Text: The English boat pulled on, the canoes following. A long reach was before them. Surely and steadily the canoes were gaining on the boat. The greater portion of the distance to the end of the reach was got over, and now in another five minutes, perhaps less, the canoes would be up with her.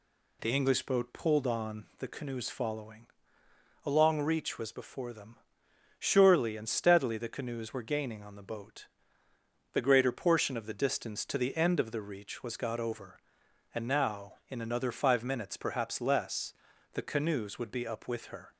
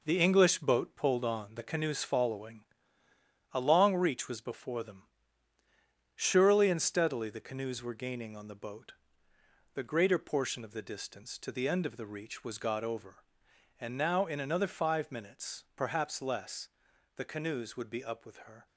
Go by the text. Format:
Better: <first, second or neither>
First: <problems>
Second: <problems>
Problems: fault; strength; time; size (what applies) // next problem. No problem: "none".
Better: first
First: none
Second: gets quieter; throughout; 7 dB